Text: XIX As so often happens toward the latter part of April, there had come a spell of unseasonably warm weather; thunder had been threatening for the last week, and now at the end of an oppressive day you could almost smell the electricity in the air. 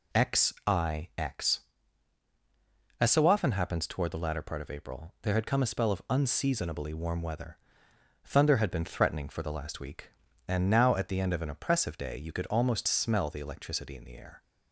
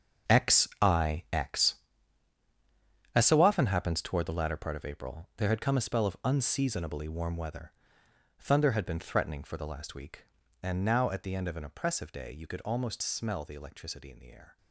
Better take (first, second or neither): first